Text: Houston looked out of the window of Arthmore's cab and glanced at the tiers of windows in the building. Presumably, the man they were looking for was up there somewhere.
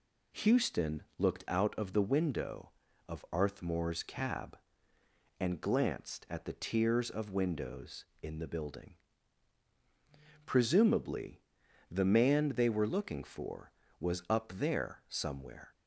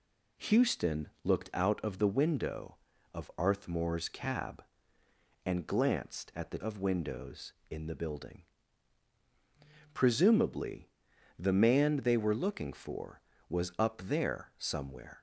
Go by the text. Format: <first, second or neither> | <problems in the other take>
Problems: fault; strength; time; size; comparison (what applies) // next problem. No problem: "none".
first | skips "tiers"; at 6.5 s